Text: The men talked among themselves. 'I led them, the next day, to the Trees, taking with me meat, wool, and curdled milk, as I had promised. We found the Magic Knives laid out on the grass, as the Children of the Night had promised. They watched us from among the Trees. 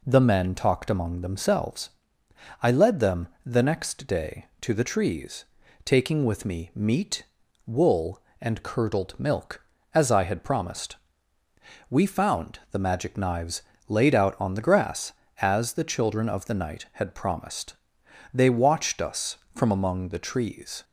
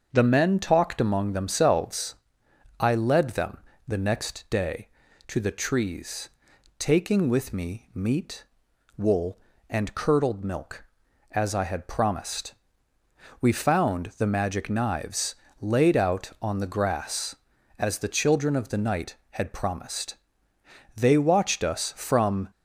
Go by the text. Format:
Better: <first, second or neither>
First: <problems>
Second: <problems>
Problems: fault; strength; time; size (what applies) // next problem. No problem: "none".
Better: first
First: pauses between "Knives" and "laid"; slight; at 13.6 s; 0.26 s long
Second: starts louder than the rest; until 1.1 s; 6.5 dB // pauses between "Knives" and "laid"; slight; at 15.3 s; 0.26 s long // stops before "among the Trees"; at 22.5 s